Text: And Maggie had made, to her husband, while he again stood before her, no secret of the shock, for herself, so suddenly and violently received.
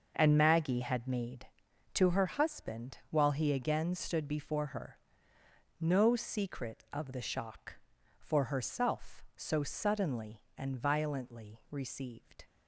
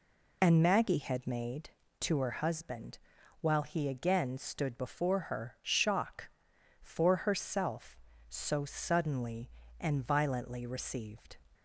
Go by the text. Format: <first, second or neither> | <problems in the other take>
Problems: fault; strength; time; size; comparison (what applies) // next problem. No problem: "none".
first | skips "no secret of the"; at 5.5 s